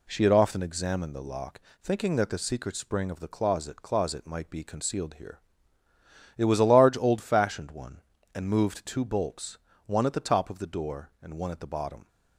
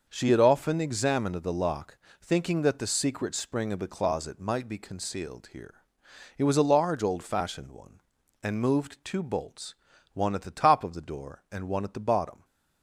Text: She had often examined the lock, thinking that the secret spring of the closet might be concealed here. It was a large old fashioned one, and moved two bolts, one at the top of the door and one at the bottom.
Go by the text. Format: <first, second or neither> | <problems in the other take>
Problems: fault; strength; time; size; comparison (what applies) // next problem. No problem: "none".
second | says "closet" twice; at 3.8 s